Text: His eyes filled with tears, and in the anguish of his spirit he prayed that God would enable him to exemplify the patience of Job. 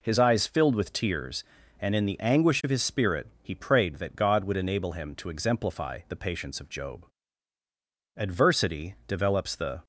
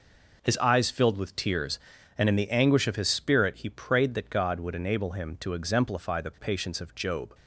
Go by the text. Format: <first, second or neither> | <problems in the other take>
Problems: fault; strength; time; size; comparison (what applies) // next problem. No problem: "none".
second | pauses between "spirit" and "he"; slight; at 3.2 s; 0.16 s long // goes on to say "Adversity develops the"; strong; from 8.1 s on; 1.6 s long